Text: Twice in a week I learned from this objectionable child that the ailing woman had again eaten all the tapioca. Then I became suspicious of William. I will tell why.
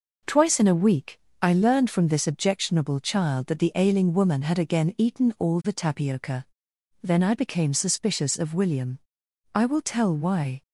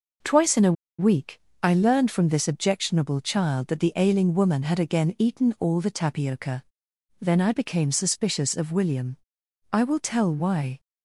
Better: first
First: pauses between "week" and "I"; slight; at 1.1 s; 0.22 s long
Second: pauses between "a" and "week"; slight; at 0.7 s; 0.26 s long // pauses between "week" and "I"; slight; at 1.3 s; 0.22 s long

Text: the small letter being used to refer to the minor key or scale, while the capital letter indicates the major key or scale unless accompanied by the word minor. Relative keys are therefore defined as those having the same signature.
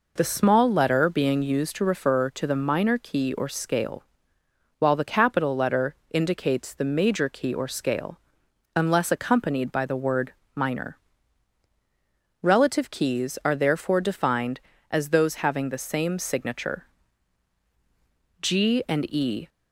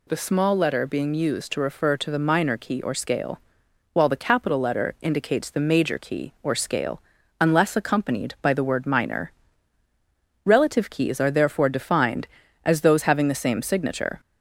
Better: second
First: pauses between "letter" and "indicates"; slight; at 5.9 s; 0.16 s long // pauses between "scale" and "unless"; noticeable; at 8.1 s; 0.56 s long // pauses between "word" and "minor"; slight; at 10.3 s; 0.20 s long // goes on to say "G and e"; noticeable; from 18.4 s on; 1.0 s long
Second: pauses between "scale" and "unless"; at 7.0 s; 0.38 s long

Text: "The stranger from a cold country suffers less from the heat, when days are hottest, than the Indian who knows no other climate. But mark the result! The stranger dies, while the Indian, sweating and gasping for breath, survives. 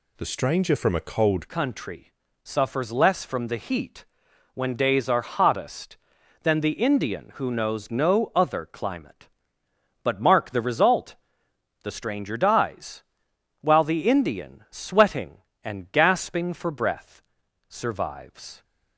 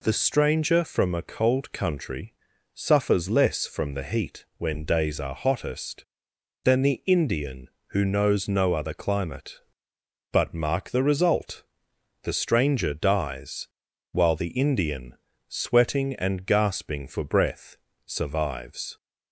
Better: second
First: changes voice at "country"; from 1.4 s on; 17.2 s long // pauses between "country" and "suffers"; slight; at 2.1 s; 0.32 s long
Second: pauses between "country" and "suffers"; at 2.3 s; 0.40 s long

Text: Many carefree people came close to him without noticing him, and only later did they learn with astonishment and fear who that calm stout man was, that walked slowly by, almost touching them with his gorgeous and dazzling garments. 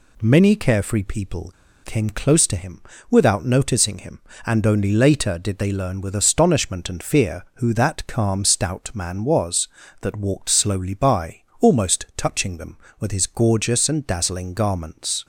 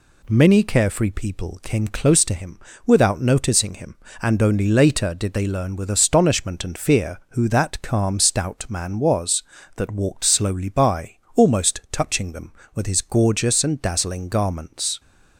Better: second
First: pauses between "people" and "came"; slight; at 1.5 s; 0.33 s long // pauses between "him" and "without"; slight; at 2.8 s; 0.26 s long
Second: pauses between "him" and "without"; slight; at 2.6 s; 0.24 s long

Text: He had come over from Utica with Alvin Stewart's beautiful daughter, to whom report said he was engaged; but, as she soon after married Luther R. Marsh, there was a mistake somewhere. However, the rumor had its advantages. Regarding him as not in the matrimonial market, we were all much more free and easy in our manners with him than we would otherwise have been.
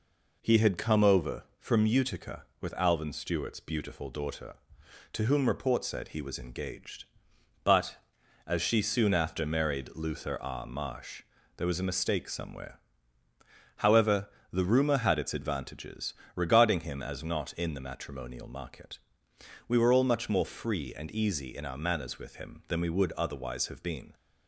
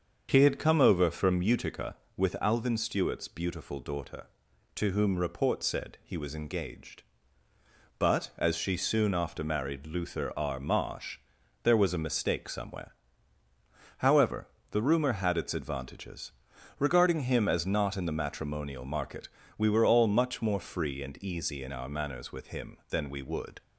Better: first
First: none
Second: starts louder than the rest; until 1.3 s; 7 dB // stops before "otherwise have been"; at 23.6 s

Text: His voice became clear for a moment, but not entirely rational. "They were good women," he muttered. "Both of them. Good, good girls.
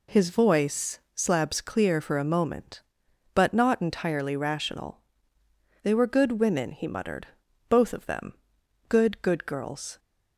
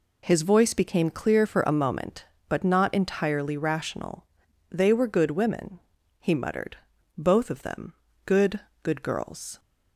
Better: second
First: says "slabs" for "became"; at 1.1 s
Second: none

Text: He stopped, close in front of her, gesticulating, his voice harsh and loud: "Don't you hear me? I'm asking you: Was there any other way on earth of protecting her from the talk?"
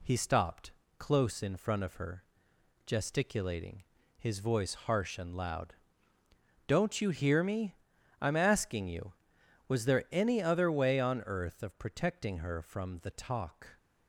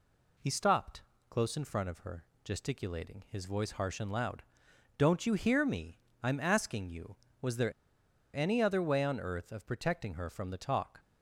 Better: first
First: none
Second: pauses between "there" and "any"; noticeable; at 7.7 s; 0.62 s long

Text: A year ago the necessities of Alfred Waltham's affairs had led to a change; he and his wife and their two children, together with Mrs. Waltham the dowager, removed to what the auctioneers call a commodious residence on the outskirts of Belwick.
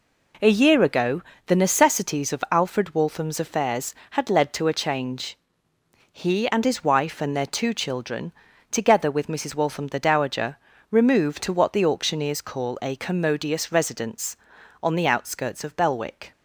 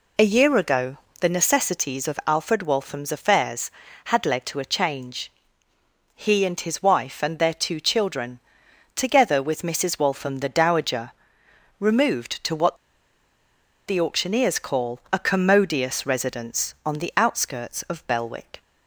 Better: first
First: pauses between "ago" and "the"; slight; at 1.2 s; 0.24 s long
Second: pauses between "ago" and "the"; slight; at 0.9 s; 0.24 s long // pauses between "what" and "the"; at 12.7 s; 1.1 s long

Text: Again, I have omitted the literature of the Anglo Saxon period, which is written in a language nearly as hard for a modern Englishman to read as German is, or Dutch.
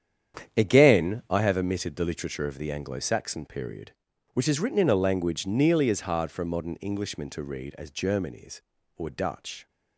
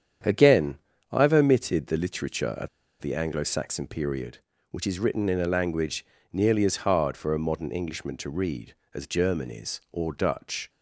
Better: first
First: starts louder than the rest; strong; until 1.6 s; 9 dB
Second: starts louder than the rest; strong; until 1.5 s; 8.5 dB // pauses between "of" and "the"; slight; at 2.6 s; 0.32 s long // pauses between "language" and "nearly"; slight; at 6.0 s; 0.26 s long

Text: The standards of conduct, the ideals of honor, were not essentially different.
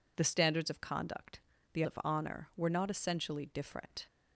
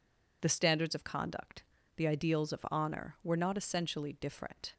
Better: second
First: skips "ideals"; at 1.8 s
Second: none

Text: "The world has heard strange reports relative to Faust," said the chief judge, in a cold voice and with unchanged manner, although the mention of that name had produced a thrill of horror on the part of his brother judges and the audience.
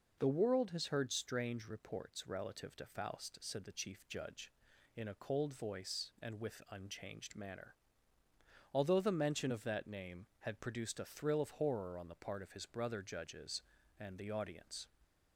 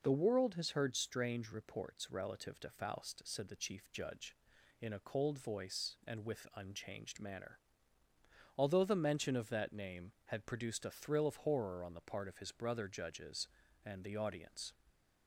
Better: neither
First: none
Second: none

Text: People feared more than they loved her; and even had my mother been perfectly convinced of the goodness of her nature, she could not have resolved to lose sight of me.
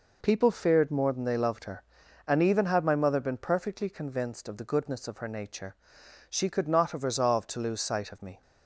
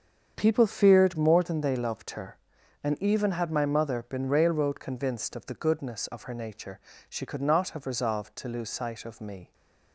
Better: first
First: none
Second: starts louder than the rest; strong; until 1.3 s; 7.5 dB // says "railroad" for "perfectly"; at 4.2 s

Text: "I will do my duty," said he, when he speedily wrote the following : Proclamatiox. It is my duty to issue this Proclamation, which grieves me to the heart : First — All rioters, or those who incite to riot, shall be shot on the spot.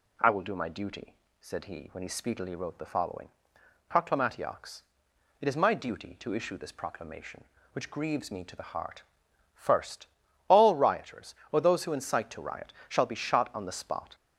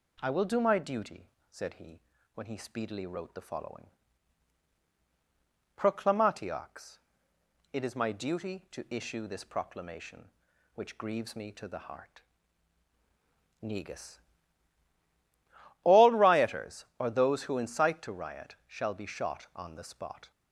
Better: first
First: none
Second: says "Negus" for "First"; at 13.6 s

